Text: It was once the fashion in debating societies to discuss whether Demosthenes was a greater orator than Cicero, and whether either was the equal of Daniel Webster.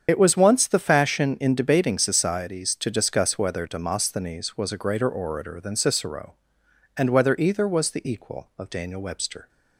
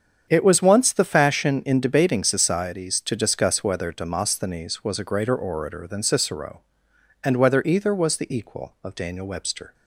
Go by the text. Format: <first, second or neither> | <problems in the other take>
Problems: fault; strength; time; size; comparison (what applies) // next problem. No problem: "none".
second | loses the start of "It"; at 0.0 s; 50 ms // starts louder than the rest; strong; until 1.0 s; 7.5 dB; strong in the second